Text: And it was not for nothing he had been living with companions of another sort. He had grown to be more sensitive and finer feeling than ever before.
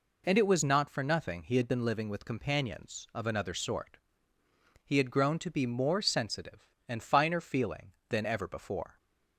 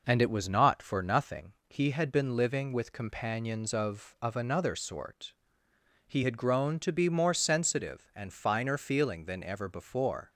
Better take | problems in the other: first | pauses between "nothing" and "he"; slight; at 1.5 s; 0.16 s long // says "of" twice; at 4.2 s

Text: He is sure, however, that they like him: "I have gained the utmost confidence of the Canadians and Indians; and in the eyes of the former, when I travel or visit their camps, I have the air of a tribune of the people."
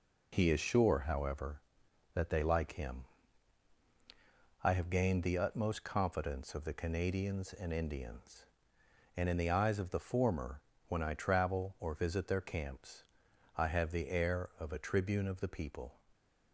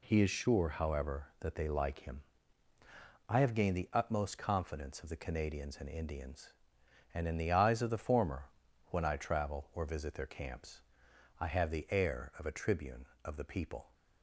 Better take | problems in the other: neither | none

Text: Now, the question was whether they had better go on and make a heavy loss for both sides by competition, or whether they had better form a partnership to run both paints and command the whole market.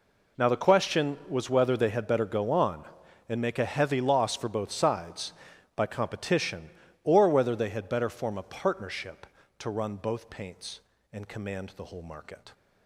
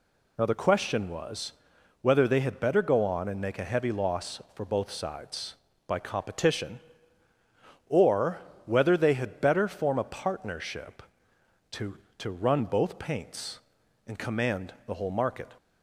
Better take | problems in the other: first | pauses between "was" and "whether"; noticeable; at 1.5 s; 0.50 s long // pauses between "or" and "whether"; slight; at 8.3 s; 0.26 s long // says "to" twice; at 12.1 s

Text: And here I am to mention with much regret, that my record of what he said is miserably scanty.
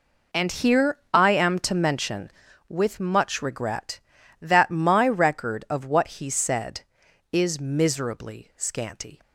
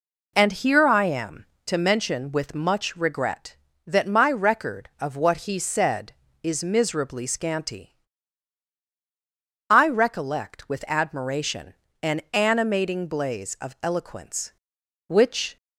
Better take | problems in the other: first | goes on to say "I recollect with admiration an animating blaze of eloquence which"; strong; from 9.7 s on; 5.8 s long

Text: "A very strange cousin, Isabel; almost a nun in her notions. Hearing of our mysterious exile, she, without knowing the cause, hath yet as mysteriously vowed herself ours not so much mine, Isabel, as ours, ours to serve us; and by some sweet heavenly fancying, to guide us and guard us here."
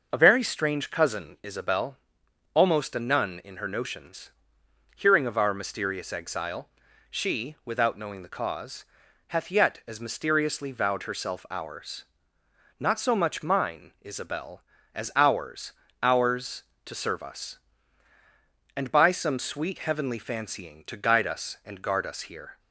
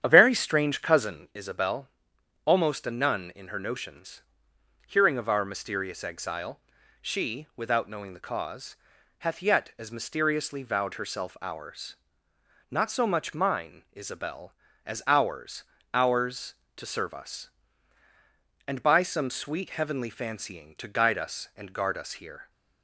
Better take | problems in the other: first | starts louder than the rest; strong; until 1.2 s; 9 dB // pauses between "ours" and "not"; noticeable; at 11.9 s; 0.74 s long; noticeable in the first

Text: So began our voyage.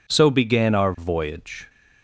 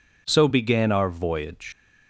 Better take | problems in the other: first | leaves "voyage" unfinished; at 1.7 s; 115 ms

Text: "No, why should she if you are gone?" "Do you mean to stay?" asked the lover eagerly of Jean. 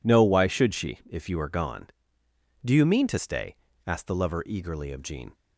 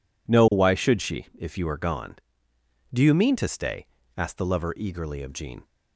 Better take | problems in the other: neither | none

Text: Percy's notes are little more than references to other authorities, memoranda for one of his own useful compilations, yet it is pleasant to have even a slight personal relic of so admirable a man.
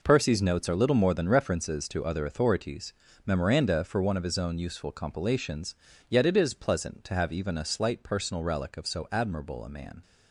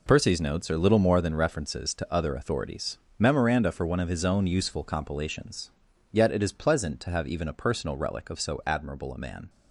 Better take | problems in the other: first | skips "slight"; at 7.5 s

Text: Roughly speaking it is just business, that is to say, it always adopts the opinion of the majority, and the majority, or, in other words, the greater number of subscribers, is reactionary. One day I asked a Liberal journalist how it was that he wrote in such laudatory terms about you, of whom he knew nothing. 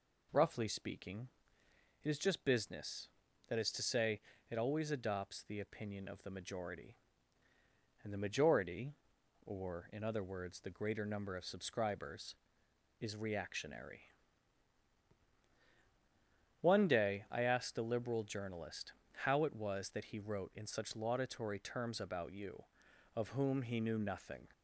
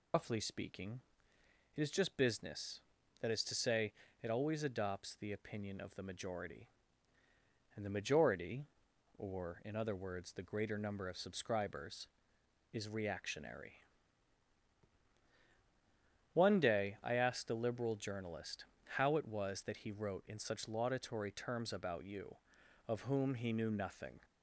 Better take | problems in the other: first | loses the start of "Roughly"; at 0.1 s; 110 ms // pauses between "speaking" and "it"; noticeable; at 1.0 s; 0.74 s long; noticeable in the first // pauses between "journalist" and "how"; slight; at 18.6 s; 0.30 s long; slight in the first

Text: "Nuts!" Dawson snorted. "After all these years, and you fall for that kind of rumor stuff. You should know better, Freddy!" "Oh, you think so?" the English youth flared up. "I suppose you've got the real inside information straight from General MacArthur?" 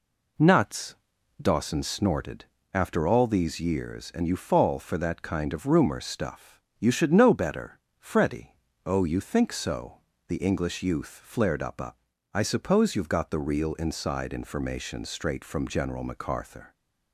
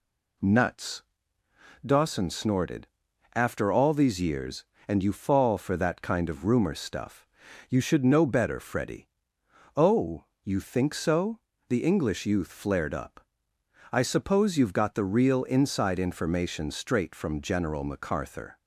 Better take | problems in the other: second | says "up" twice; at 11.7 s

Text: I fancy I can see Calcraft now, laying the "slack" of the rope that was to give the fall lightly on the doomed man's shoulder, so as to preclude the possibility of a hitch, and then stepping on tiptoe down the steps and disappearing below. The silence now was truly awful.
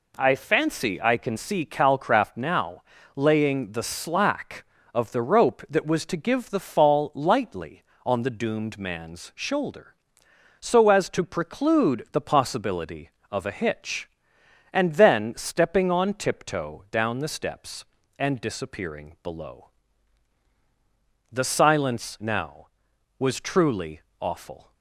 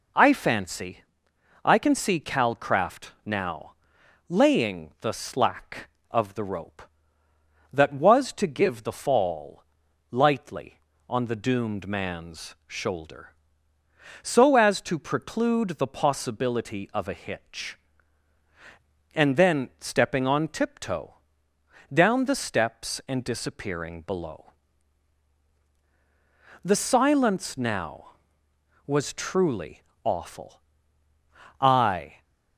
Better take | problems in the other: first | pauses between "fancy" and "I"; noticeable; at 1.0 s; 0.62 s long // pauses between "fall" and "lightly"; noticeable; at 9.6 s; 0.46 s long // pauses between "tiptoe" and "down"; noticeable; at 21.1 s; 0.80 s long // pauses between "truly" and "awful"; slight; at 29.8 s; 0.22 s long; slight in the first // goes on to say "I"; noticeable; from 31.6 s on; 0.62 s long

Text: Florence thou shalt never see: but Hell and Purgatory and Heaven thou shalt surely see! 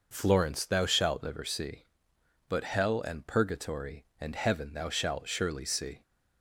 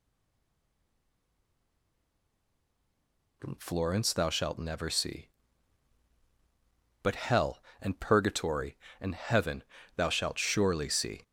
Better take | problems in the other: first | stays silent before the first word; strong; until 3.4 s; 3.4 s long // pauses between "Heaven" and "thou"; slight; at 9.6 s; 0.32 s long

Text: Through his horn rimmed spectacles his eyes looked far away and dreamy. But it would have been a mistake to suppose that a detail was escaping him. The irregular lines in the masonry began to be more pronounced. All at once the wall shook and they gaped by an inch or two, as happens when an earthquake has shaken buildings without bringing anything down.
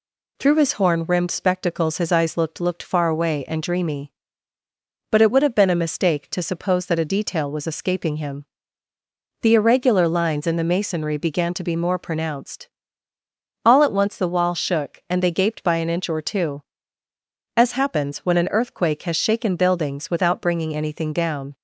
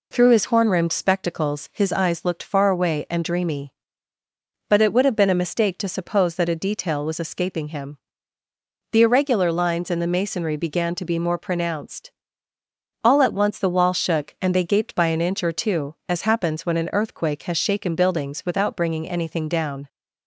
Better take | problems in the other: second | says "looked" twice; at 2.5 s

